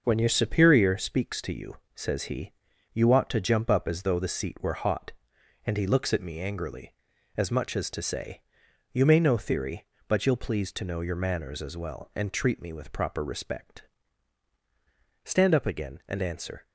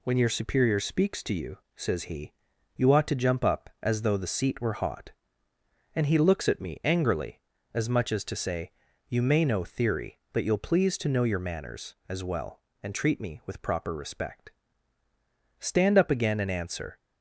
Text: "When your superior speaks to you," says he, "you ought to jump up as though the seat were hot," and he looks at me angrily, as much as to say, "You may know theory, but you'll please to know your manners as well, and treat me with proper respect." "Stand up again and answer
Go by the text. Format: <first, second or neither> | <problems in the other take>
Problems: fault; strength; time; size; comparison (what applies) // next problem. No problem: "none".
neither | none